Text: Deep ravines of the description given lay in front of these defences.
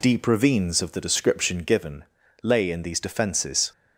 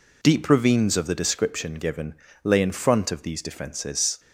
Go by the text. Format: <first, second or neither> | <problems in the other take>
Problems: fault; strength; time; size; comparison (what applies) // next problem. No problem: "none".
second | pauses between "given" and "lay"; at 2.0 s; 0.38 s long; slight in the second // skips "front of"; at 2.8 s